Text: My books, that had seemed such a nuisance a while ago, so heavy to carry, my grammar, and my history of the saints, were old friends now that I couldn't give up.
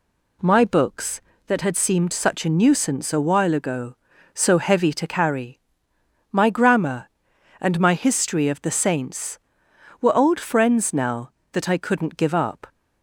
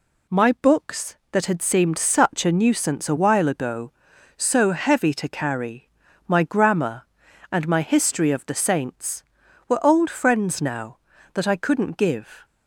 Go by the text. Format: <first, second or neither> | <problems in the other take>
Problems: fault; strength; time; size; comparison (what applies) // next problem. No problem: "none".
first | stops before "up"; at 12.4 s